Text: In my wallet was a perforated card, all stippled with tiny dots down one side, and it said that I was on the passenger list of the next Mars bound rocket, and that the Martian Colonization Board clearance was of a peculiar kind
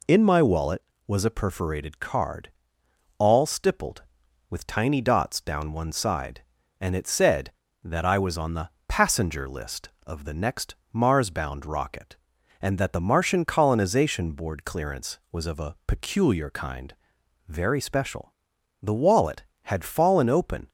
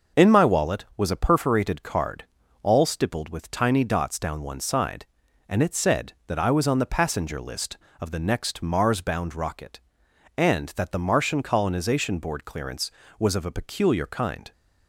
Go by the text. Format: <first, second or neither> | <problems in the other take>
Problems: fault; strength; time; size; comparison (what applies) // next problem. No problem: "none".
second | pauses between "the" and "passenger"; slight; at 8.7 s; 0.18 s long // pauses between "next" and "Mars"; slight; at 10.7 s; 0.18 s long // goes on to say "very special The wallet had fallen open"; strong; from 17.4 s on; 3.2 s long